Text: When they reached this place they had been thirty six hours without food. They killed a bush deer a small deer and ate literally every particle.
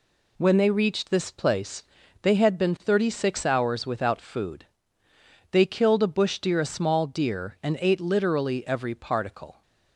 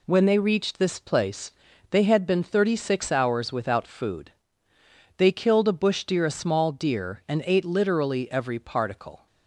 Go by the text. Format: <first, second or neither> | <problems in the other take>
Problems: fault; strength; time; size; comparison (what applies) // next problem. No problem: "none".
neither | pauses between "place" and "they"; the same in both